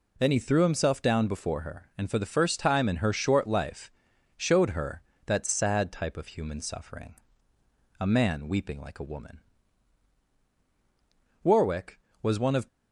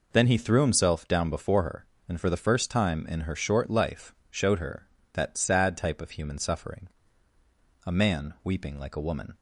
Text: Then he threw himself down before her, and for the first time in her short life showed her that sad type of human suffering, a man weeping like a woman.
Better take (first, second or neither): second